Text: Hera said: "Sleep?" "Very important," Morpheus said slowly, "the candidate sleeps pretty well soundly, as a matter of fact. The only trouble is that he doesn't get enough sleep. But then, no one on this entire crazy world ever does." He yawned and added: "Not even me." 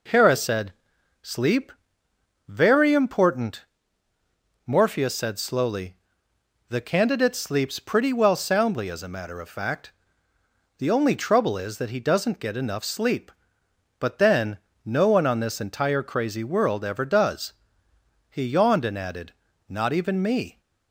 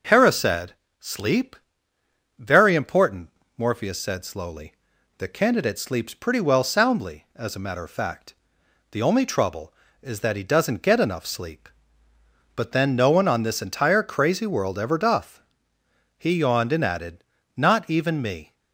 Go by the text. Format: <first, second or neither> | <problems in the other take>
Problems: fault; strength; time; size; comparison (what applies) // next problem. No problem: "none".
first | says "doth" for "does"; at 14.9 s